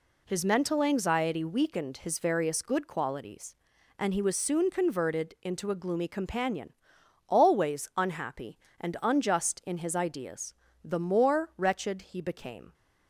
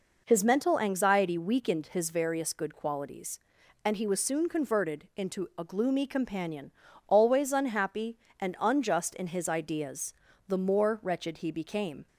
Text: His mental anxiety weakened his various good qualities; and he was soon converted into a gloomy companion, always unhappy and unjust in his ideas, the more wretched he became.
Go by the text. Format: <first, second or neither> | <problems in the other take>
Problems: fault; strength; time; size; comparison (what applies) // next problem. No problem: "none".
neither | none